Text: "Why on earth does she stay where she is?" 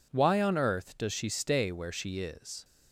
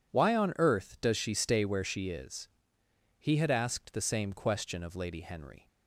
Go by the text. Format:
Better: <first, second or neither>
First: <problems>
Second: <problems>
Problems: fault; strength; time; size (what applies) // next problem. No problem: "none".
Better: first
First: none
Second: goes on to say "He had asked the same question of Lady Henry"; strong; from 3.1 s on; 2.4 s long